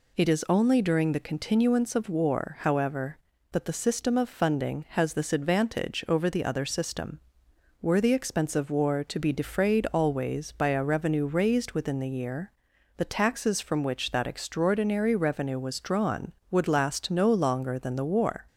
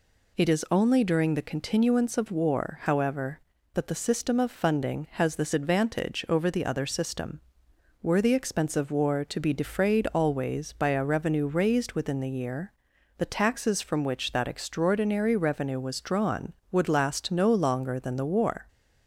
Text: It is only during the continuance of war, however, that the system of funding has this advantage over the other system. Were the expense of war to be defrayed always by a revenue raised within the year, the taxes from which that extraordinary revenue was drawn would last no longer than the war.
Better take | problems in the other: neither | none

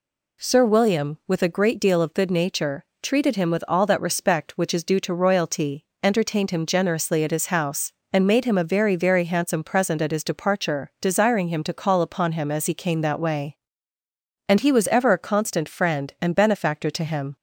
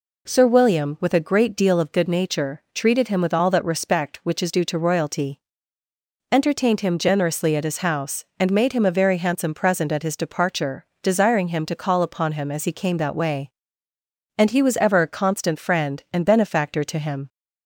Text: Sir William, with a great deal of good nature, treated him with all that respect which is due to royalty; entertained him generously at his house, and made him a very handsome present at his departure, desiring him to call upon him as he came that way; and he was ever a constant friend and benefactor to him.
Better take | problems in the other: second | says "very" twice; at 8.9 s

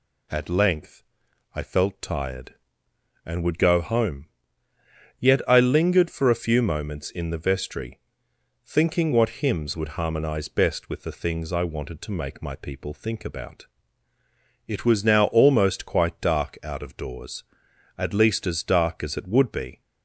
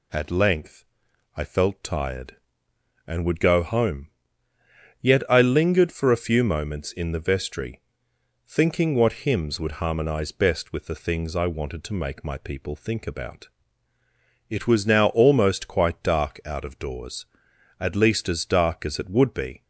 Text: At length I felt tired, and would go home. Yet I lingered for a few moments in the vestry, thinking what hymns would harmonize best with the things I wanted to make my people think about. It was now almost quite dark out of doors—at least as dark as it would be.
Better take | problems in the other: neither | pauses between "length" and "I"; noticeable; the same in both

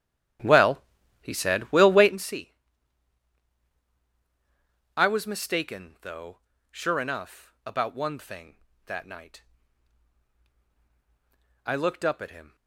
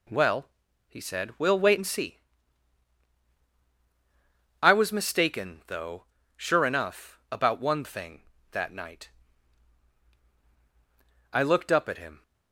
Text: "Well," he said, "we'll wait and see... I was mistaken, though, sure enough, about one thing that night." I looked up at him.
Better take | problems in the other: second | starts louder than the rest; strong; until 2.2 s; 10.5 dB

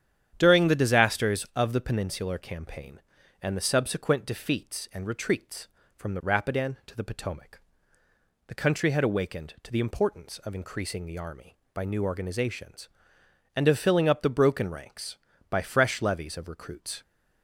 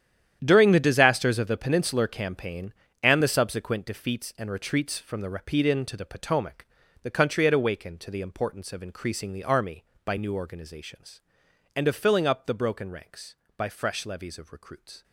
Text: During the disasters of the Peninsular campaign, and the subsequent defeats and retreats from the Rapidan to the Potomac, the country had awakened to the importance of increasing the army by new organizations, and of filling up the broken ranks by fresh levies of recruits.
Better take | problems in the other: first | gets quieter; strong; throughout; 13.5 dB // starts louder than the rest; strong; until 1.4 s; 10 dB; strong in the first

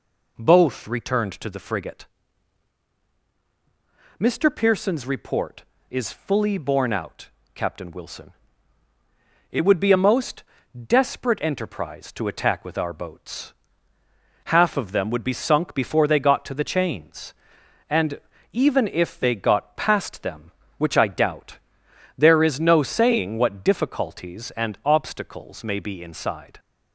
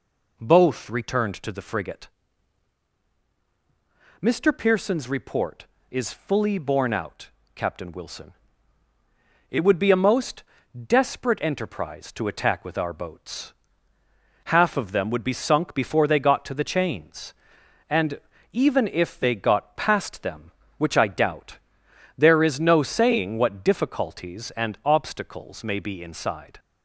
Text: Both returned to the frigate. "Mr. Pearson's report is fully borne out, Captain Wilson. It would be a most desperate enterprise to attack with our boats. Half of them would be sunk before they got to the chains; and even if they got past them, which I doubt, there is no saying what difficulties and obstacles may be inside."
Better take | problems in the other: neither | pauses between "most" and "desperate"; noticeable; the same in both // pauses between "and" and "even"; slight; the same in both

